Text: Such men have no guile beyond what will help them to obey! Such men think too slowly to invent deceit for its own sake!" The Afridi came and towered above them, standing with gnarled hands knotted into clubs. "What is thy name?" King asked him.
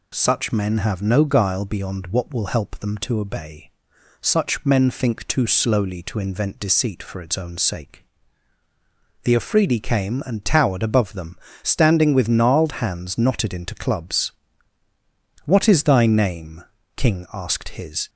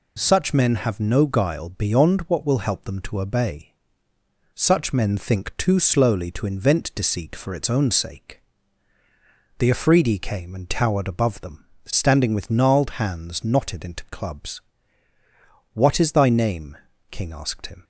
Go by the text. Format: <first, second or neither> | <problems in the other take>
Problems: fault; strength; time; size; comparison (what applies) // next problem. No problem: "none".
second | says "his" for "him"; at 17.7 s